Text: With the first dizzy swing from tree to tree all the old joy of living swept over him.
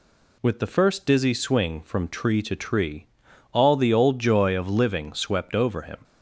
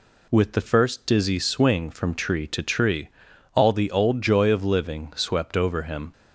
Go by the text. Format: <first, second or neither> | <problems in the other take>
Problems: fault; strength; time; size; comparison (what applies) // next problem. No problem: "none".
neither | pauses between "tree" and "all"; noticeable; the same in both